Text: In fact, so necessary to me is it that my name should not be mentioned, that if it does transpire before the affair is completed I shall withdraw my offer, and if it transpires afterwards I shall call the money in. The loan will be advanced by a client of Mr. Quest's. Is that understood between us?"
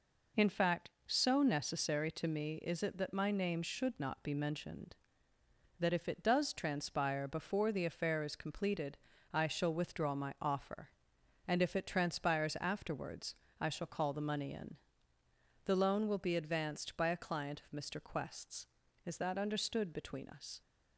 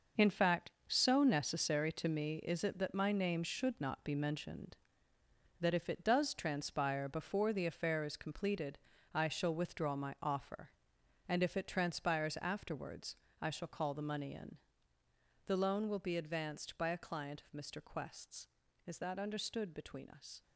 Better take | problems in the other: first | gets quieter; strong; throughout; 10.5 dB // pauses between "completed" and "I"; slight; at 8.7 s; 0.36 s long; slight in the first // pauses between "afterwards" and "I"; slight; at 13.1 s; 0.26 s long; slight in the first

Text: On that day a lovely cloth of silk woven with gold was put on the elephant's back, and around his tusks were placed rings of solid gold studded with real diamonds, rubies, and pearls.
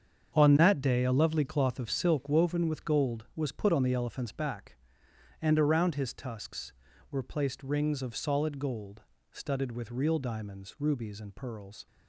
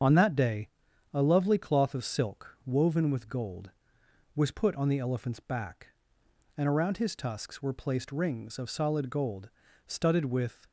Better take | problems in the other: first | starts louder than the rest; strong; until 1.5 s; 7.5 dB; strong in the first // pauses between "day" and "a"; noticeable; at 0.6 s; 0.48 s long // pauses between "gold" and "studded"; slight; at 9.5 s; 0.36 s long; slight in the first // stops before "real diamonds rubies and pearls"; at 10.6 s

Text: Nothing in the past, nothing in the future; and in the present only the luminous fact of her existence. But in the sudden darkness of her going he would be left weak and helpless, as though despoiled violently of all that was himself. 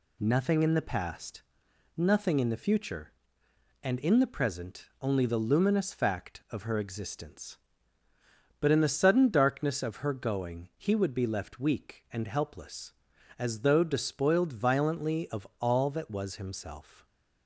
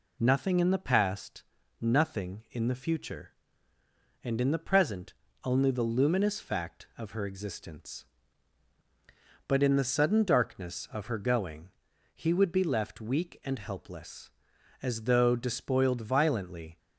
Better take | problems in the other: first | pauses between "present" and "only"; slight; at 5.1 s; 0.32 s long; slight in the first // pauses between "going" and "he"; at 11.6 s; 0.44 s long // stops before "of all that was himself"; at 16.7 s

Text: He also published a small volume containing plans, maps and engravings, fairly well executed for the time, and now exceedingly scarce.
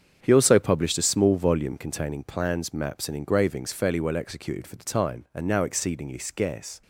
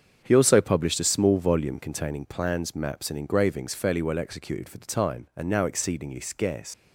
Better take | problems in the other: first | starts louder than the rest; strong; until 1.2 s; 7.5 dB; strong in the first // leaves "scarce" unfinished; at 6.7 s; 95 ms

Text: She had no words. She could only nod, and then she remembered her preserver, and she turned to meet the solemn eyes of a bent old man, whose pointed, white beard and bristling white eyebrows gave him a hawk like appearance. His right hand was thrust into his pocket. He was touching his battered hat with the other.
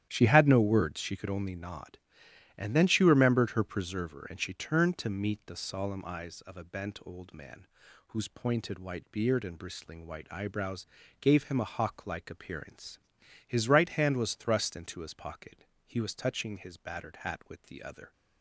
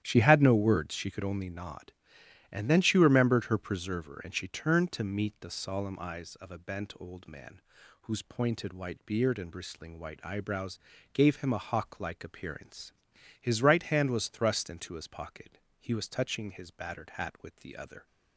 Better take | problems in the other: neither | starts louder than the rest; strong; the same in both // pauses between "eyebrows" and "gave"; slight; the same in both

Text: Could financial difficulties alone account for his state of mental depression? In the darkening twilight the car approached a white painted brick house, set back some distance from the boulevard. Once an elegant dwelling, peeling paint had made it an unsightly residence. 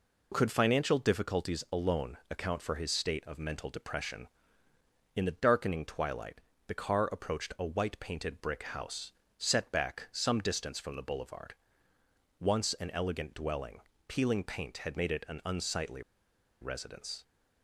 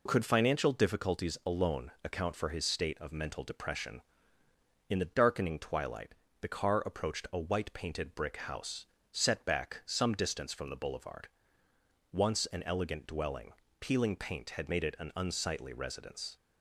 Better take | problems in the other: second | pauses between "twilight" and "the"; slight; at 6.4 s; 0.26 s long; slight in the second // pauses between "unsightly" and "residence"; noticeable; at 16.0 s; 0.60 s long

